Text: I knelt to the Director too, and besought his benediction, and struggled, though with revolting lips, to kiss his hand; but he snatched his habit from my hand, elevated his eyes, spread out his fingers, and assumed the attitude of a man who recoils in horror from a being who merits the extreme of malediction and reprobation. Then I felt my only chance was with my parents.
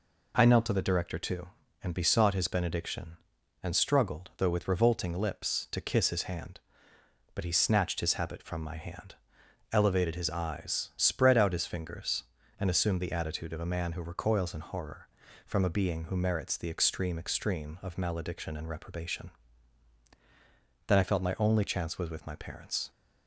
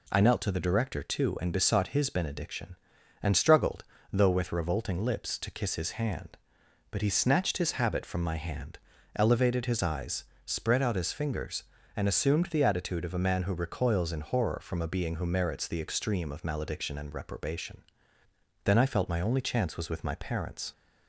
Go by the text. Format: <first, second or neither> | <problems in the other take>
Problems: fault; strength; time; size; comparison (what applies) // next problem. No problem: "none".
second | says "extreme" twice; at 17.1 s